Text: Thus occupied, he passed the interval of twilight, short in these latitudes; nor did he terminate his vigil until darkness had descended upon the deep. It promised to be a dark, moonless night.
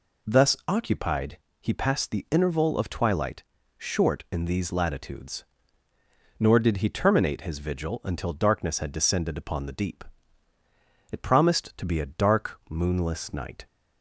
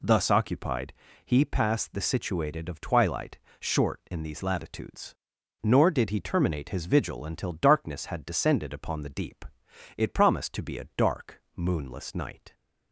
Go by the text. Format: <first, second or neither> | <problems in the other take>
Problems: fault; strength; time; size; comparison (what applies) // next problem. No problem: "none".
first | says "situated" for "interval"; at 2.0 s